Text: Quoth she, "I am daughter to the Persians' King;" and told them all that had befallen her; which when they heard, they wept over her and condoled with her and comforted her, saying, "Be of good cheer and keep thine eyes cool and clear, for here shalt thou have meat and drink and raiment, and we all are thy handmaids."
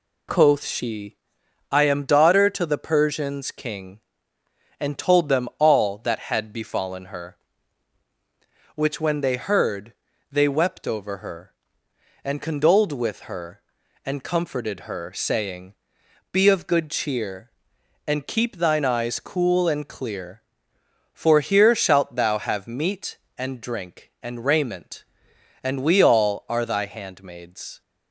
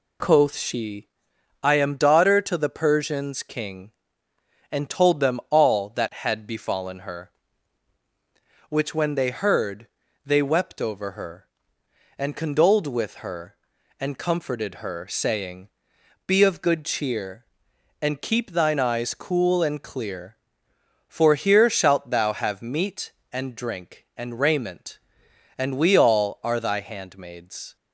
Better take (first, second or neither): neither